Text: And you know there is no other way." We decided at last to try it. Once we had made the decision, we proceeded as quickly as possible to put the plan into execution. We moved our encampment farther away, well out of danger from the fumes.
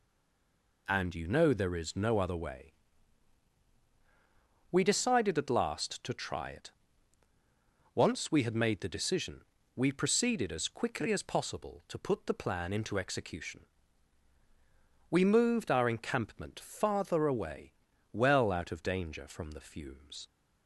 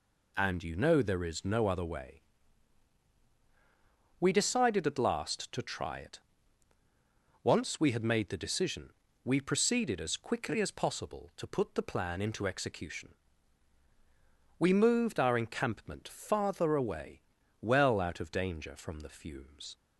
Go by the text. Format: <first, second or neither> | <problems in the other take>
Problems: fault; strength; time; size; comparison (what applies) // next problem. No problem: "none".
second | stays silent before the first word; slight; until 0.8 s; 0.8 s long